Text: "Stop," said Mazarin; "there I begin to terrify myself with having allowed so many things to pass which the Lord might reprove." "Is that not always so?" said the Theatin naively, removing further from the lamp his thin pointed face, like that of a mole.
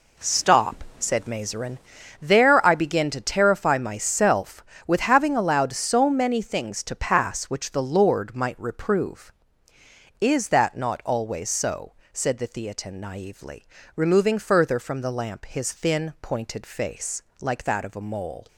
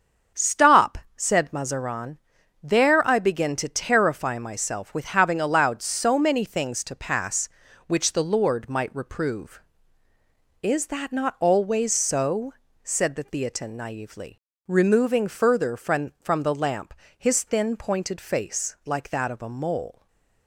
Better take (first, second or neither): first